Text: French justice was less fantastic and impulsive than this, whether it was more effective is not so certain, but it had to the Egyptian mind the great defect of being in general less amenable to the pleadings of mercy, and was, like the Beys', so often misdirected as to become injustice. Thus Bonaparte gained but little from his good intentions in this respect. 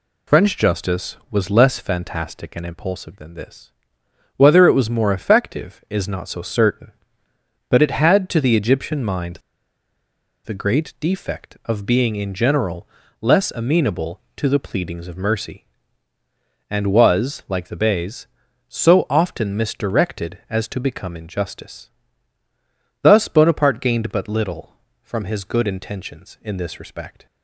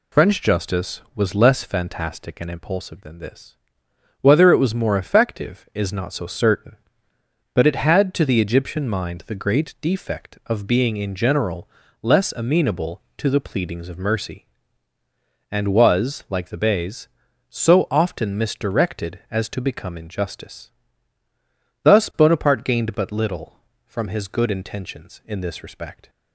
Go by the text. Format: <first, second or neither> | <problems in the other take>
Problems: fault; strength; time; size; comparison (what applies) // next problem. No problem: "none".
second | pauses between "mind" and "the"; at 9.3 s; 1.0 s long // pauses between "general" and "less"; slight; at 12.8 s; 0.36 s long; slight in the second